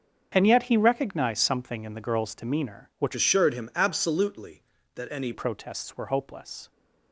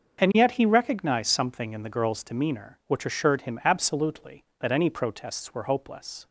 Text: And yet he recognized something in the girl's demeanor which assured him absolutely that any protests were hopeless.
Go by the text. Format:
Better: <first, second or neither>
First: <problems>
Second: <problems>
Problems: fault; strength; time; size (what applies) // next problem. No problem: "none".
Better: second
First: starts louder than the rest; until 1.3 s; 6.5 dB // changes voice from "assured" to "any"; from 3.1 to 5.3 s; 2.2 s long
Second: starts louder than the rest; until 1.2 s; 6.5 dB